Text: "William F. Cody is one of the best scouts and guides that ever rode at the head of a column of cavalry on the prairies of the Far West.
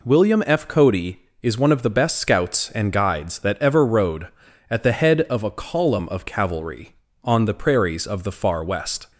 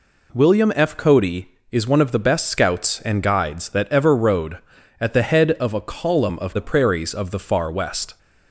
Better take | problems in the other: first | skips "cavalry on"; at 6.5 s

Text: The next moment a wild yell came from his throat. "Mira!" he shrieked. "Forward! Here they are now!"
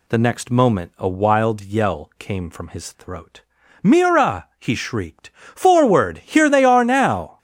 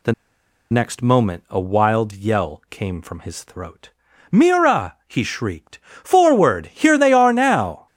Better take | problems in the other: first | pauses between "The" and "next"; noticeable; at 0.1 s; 0.57 s long

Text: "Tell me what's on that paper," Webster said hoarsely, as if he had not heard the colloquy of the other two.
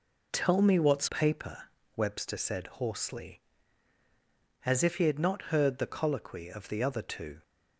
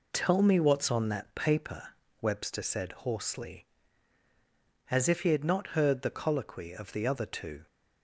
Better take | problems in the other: second | skips "on that"; at 1.0 s

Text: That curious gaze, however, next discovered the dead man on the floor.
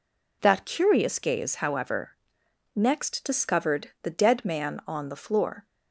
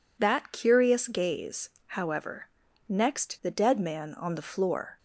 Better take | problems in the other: first | skips "discovered"; at 3.4 s

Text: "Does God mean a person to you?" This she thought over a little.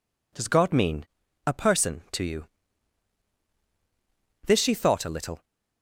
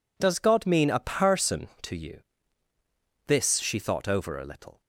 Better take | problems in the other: second | pauses between "mean" and "a"; at 1.0 s; 0.40 s long // skips "over"; at 5.0 s

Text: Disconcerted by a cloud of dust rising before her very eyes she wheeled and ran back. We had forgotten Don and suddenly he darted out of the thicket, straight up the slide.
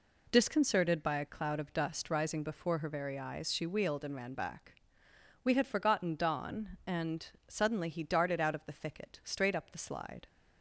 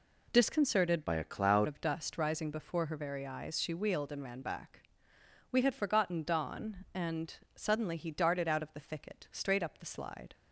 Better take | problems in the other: first | changes voice from "by" to "cloud"; from 1.0 to 1.6 s; 0.6 s long // pauses between "and" and "suddenly"; slight; at 7.3 s; 0.22 s long; slight in the first

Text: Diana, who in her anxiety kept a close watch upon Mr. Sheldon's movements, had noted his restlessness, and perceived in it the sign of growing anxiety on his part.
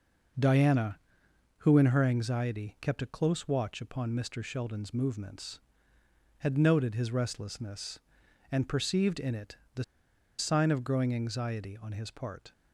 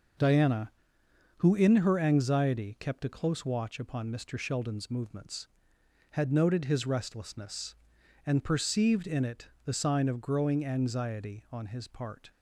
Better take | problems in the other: second | pauses between "it" and "the"; slight; at 9.5 s; 0.18 s long; slight in the second // pauses between "the" and "sign"; noticeable; at 9.8 s; 0.54 s long

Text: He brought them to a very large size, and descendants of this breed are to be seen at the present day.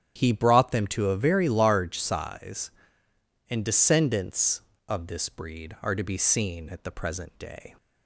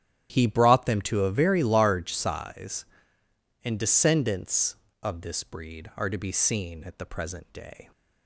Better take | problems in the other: first | gets quieter; strong; throughout; 17 dB // starts louder than the rest; strong; until 1.3 s; 11 dB; strong in the first

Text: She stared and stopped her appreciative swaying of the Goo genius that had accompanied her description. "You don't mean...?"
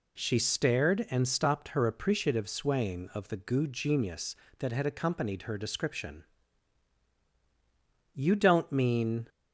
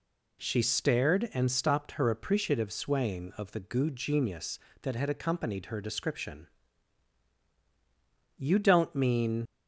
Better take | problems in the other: first | leaves "mean" unfinished; at 9.4 s; 60 ms

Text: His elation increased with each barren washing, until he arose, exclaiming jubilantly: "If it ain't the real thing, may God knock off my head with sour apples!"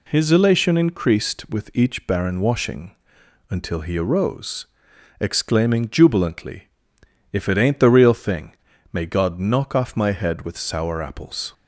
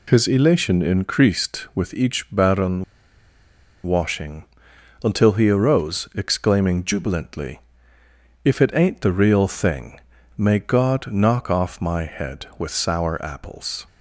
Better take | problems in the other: first | pauses between "barren" and "washing"; at 2.8 s; 1.0 s long

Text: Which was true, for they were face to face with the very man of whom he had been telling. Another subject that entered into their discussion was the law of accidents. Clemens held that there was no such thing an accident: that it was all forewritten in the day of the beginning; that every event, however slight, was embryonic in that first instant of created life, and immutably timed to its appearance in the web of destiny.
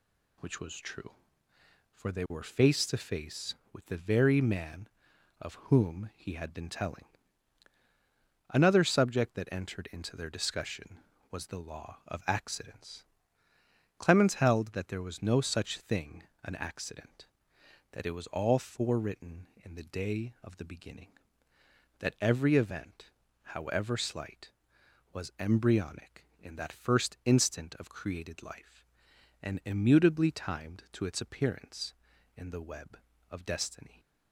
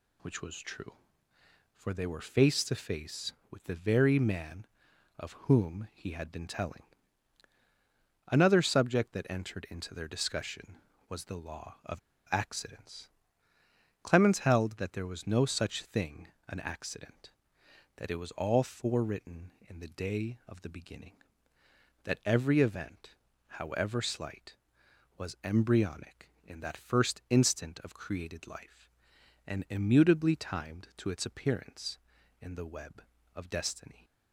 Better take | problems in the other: first | pauses between "of" and "accidents"; slight; at 11.9 s; 0.30 s long // pauses between "thing" and "an"; slight; at 16.2 s; 0.20 s long; slight in the first

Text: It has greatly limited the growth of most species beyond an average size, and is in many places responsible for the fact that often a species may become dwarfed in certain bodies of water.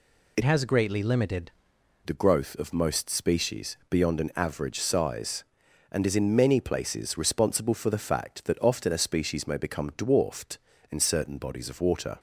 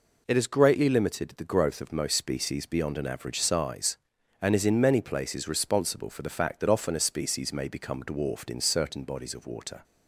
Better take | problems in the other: second | changes voice from "has" to "limited"; from 0.4 to 1.5 s; 1.1 s long

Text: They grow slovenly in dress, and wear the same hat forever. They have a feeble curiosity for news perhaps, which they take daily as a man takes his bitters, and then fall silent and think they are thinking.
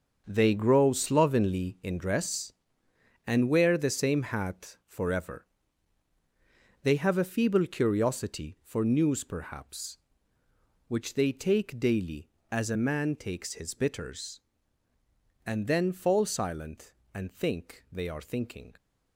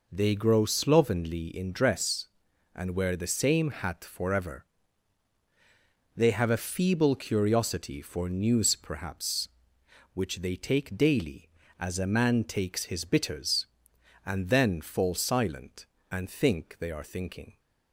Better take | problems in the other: second | gets quieter; strong; throughout; 10.5 dB

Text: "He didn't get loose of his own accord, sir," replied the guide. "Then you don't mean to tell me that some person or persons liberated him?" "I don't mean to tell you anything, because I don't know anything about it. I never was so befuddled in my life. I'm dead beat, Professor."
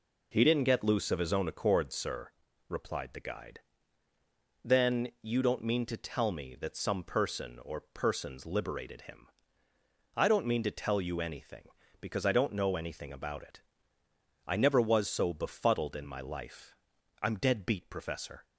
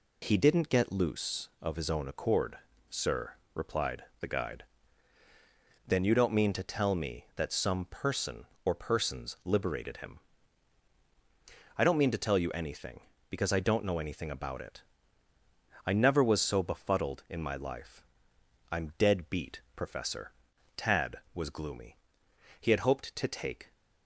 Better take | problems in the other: first | pauses between "replied" and "the"; slight; at 4.0 s; 0.16 s long // goes on to say "Tad was gloomy He had hoped to take"; strong; from 20.7 s on; 2.9 s long

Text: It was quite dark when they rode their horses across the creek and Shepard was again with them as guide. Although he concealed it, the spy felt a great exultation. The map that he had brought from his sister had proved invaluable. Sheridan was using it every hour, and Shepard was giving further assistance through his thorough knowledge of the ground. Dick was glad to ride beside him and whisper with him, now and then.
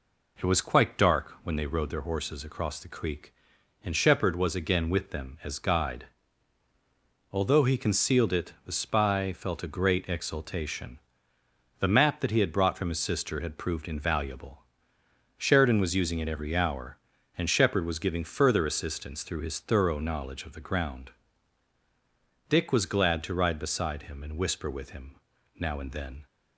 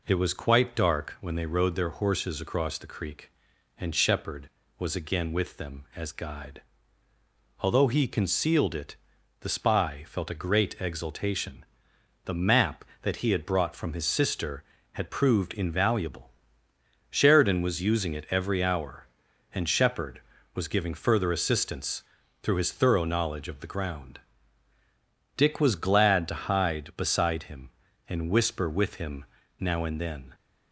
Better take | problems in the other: first | pauses between "assistance" and "through"; at 22.0 s; 0.40 s long // says "hide" for "ride"; at 26.3 s

